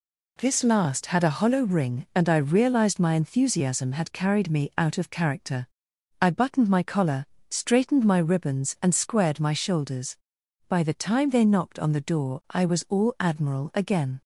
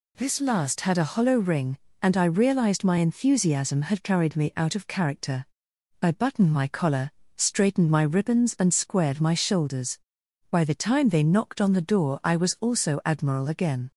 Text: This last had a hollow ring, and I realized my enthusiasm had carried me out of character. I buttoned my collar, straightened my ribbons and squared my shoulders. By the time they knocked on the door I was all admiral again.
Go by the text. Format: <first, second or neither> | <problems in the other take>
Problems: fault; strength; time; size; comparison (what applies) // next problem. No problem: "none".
first | says "also" for "all"; at 12.6 s